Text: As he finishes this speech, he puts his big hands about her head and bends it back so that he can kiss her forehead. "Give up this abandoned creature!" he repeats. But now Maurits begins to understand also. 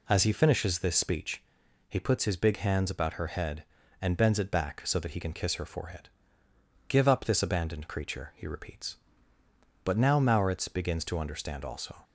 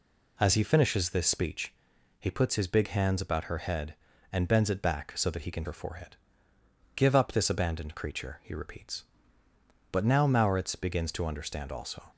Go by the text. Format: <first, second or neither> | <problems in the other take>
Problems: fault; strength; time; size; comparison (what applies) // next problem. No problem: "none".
first | skips "kiss"; at 5.6 s